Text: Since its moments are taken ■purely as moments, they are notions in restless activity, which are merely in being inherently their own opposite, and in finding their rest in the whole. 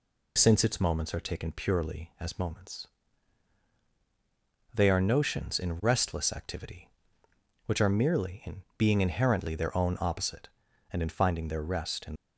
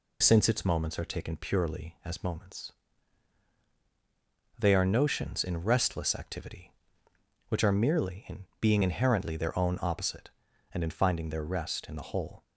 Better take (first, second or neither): second